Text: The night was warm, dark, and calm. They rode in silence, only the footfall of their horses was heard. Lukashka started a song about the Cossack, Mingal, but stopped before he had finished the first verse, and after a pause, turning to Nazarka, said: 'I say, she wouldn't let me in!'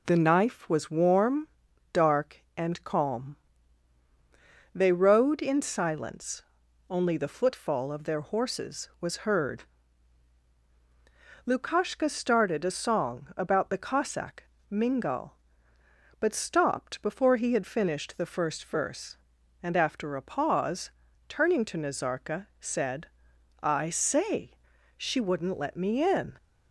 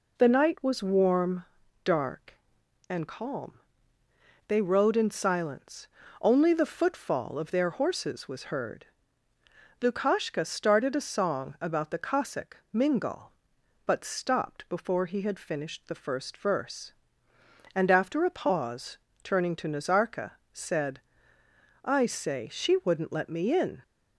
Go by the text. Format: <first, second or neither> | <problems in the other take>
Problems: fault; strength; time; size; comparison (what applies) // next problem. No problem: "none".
second | says "knife" for "night"; at 0.1 s